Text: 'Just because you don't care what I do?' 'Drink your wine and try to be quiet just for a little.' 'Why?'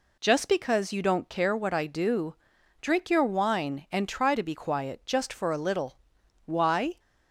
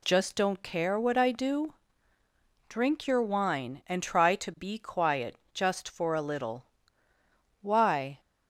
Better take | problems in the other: first | skips "because you"; at 0.3 s // pauses between "quiet" and "just"; slight; at 5.3 s; 0.16 s long

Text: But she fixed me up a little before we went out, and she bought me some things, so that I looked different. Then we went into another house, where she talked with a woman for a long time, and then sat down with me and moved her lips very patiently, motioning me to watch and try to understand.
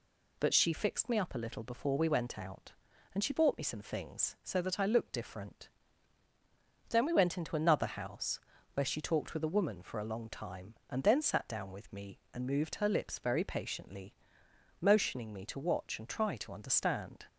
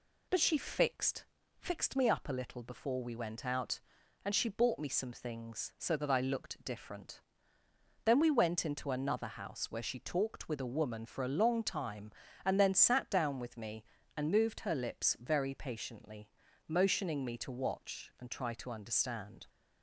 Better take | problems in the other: first | says "fixed" twice; at 1.5 s

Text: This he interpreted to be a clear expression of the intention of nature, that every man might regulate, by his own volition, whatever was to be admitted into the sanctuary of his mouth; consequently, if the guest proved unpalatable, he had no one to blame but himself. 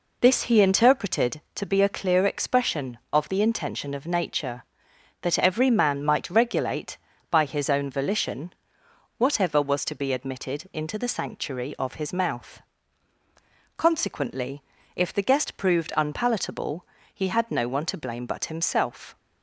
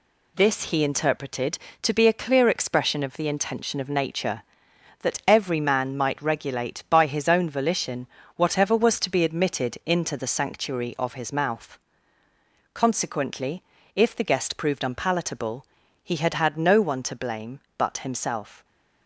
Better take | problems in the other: first | says "had" twice; at 16.3 s

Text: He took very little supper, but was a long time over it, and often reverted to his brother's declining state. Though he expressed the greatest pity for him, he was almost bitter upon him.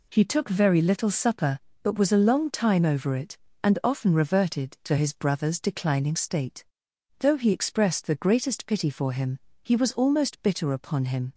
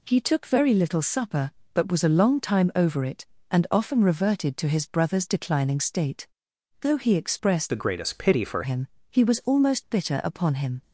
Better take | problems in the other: first | changes voice from "the" to "for"; from 7.6 to 8.6 s; 1.0 s long

